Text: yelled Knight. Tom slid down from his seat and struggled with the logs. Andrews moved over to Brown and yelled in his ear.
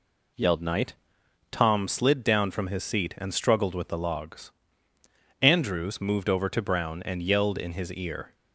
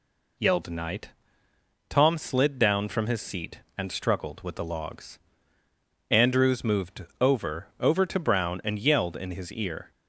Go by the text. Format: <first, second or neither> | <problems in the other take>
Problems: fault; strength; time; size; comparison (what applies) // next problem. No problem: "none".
first | says "over" twice; at 7.7 s